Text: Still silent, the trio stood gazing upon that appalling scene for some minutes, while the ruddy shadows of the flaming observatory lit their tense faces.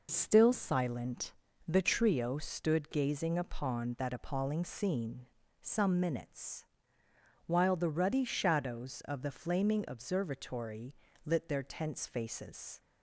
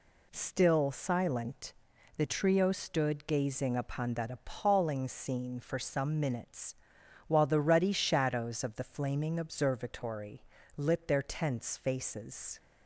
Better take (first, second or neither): second